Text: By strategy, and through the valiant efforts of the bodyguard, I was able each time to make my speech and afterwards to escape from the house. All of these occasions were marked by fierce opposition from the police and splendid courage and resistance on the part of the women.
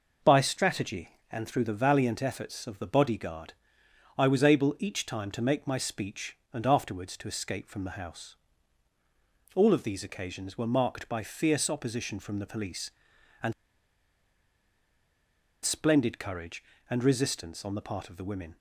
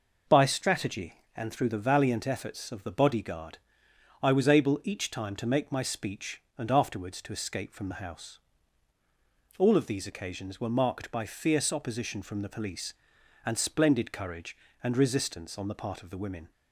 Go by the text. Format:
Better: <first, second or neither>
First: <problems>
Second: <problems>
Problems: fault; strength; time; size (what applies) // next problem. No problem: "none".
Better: second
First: pauses between "and" and "splendid"; strong; at 13.5 s; 2.1 s long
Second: none